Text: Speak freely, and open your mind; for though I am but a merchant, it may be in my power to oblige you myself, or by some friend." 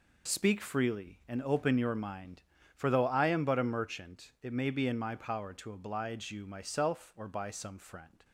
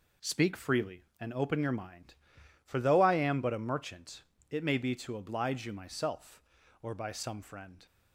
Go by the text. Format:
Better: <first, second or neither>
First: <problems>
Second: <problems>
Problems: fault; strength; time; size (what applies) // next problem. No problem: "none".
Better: first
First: none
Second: skips "in my power"; at 4.9 s